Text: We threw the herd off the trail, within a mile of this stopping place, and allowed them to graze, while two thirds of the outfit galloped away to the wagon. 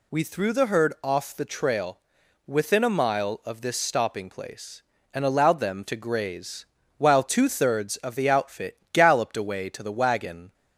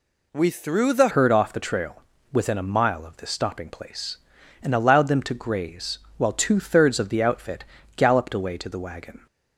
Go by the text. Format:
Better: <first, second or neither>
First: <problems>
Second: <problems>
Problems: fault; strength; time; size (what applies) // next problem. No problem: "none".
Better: first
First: none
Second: changes voice at "herd"; from 1.0 s on; 8.2 s long // pauses between "outfit" and "galloped"; slight; at 7.6 s; 0.32 s long